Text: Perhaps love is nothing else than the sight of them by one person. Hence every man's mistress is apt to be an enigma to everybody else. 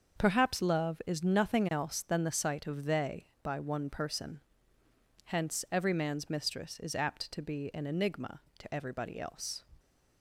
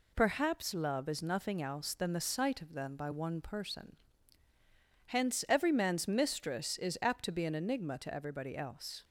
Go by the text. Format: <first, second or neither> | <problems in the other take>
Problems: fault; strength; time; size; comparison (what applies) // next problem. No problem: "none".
second | starts louder than the rest; until 1.2 s; 6.5 dB // says "they" for "them"; at 2.8 s